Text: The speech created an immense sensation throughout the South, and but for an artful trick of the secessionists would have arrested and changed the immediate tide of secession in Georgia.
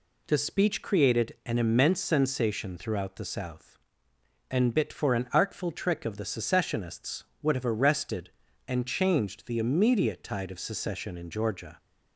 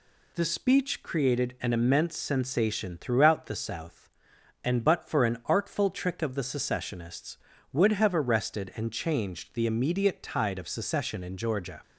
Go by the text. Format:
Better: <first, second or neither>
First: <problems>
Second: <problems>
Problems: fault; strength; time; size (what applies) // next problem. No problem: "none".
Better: second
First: says "bit" for "but"; at 4.7 s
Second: none